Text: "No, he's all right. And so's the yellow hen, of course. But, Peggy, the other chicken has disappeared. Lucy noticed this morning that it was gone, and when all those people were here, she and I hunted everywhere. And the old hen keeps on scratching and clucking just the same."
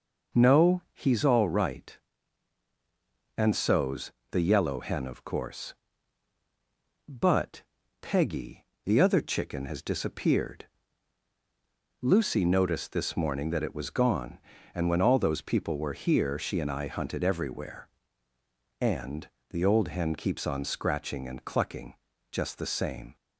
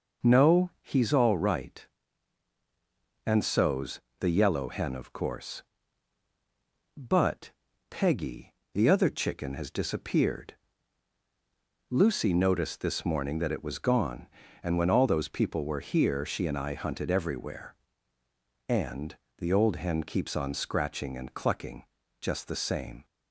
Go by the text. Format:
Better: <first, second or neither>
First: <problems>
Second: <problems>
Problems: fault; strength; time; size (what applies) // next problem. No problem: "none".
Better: neither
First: pauses between "so's" and "the"; slight; at 4.1 s; 0.18 s long // pauses between "And" and "the"; slight; at 19.2 s; 0.24 s long // pauses between "clucking" and "just"; slight; at 21.9 s; 0.36 s long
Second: pauses between "so's" and "the"; slight; at 4.0 s; 0.18 s long // pauses between "And" and "the"; slight; at 19.1 s; 0.24 s long // pauses between "clucking" and "just"; slight; at 21.8 s; 0.36 s long